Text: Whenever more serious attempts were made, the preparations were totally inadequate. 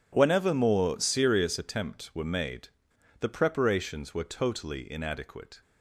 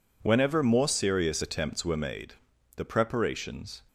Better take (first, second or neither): first